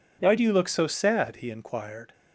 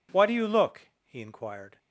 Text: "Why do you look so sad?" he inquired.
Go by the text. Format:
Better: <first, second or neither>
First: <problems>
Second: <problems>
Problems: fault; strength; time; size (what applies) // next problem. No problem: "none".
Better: first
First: none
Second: skips "so sad"; at 0.9 s